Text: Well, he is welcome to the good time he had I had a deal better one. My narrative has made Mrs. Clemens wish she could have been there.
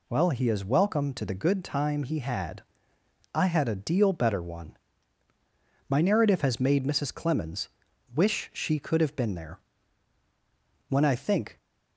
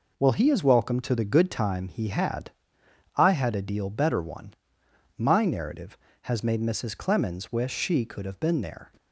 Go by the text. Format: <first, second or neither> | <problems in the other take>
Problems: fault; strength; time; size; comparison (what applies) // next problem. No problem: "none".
second | pauses between "had" and "I"; noticeable; at 2.6 s; 0.72 s long; noticeable in the second // pauses between "Clemens" and "wish"; noticeable; at 7.6 s; 0.46 s long // goes on to say "When I think"; noticeable; from 10.8 s on; 0.68 s long